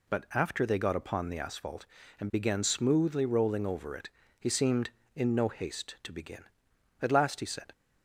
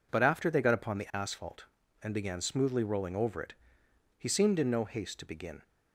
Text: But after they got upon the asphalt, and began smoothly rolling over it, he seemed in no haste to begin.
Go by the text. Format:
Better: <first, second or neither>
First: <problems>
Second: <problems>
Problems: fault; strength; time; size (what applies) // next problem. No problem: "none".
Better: second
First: goes on to say "At last he said"; noticeable; from 6.9 s on; 0.72 s long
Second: none